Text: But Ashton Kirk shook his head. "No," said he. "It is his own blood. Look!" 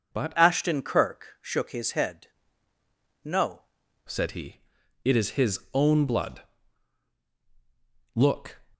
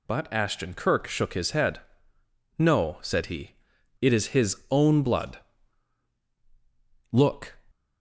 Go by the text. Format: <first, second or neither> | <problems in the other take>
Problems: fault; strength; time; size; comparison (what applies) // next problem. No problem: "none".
second | changes voice from "Ashton" to "No"; from 0.3 to 3.6 s; 3.3 s long // pauses between "his" and "own"; slight; at 5.5 s; 0.16 s long; slight in the second